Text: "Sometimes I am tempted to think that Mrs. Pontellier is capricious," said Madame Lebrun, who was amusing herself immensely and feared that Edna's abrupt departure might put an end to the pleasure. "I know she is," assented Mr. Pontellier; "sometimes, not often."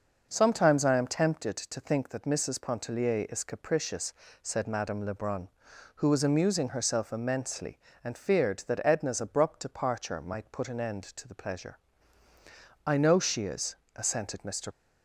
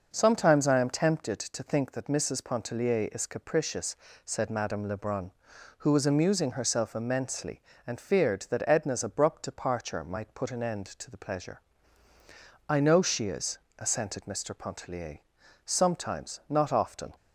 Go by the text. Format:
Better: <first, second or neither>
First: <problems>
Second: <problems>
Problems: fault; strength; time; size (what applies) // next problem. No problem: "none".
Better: second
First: stops before "Pontellier sometimes not often"; at 14.7 s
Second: none